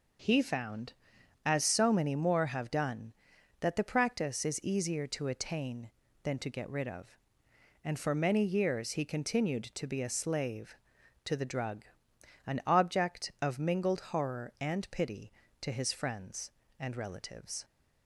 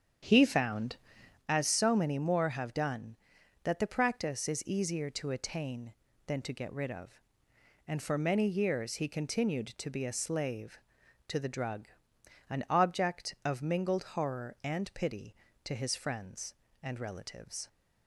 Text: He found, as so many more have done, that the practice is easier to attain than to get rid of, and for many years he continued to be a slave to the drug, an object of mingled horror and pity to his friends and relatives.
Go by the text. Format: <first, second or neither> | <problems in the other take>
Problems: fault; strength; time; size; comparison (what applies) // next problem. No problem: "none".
first | starts louder than the rest; strong; until 1.4 s; 8 dB